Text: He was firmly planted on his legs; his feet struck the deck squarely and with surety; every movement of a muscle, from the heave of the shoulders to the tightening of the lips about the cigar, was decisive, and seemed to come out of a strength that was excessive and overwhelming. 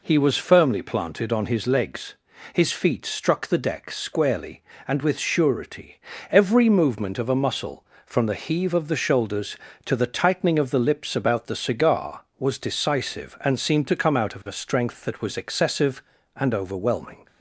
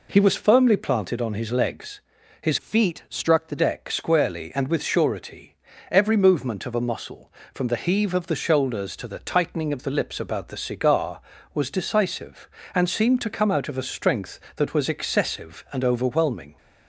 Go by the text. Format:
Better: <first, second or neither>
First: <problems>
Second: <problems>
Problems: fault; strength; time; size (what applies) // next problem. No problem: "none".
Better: first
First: none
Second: changes voice from "feet" to "the"; from 2.5 to 3.5 s; 1.0 s long